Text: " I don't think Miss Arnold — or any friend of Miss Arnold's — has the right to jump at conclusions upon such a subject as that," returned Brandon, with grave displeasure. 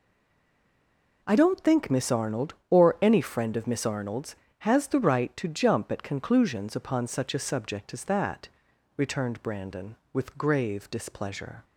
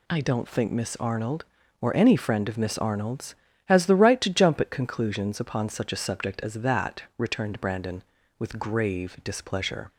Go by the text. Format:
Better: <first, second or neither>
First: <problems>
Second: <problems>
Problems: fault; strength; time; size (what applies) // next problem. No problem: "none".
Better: second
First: stays silent before the first word; noticeable; until 1.2 s; 1.2 s long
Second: none